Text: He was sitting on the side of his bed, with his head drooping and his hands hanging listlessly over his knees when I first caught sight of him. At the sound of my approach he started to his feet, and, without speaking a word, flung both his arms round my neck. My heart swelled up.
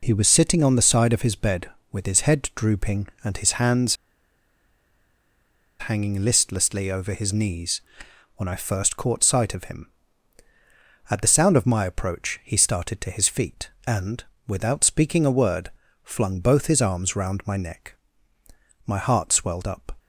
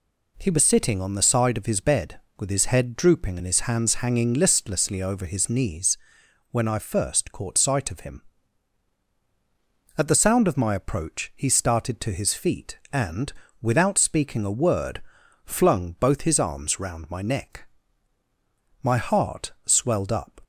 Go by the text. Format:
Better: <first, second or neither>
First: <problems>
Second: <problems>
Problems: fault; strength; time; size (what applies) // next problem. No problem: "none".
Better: second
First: pauses between "hands" and "hanging"; strong; at 3.9 s; 1.8 s long // pauses between "knees" and "when"; noticeable; at 7.7 s; 0.56 s long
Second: pauses between "knees" and "when"; noticeable; at 5.9 s; 0.54 s long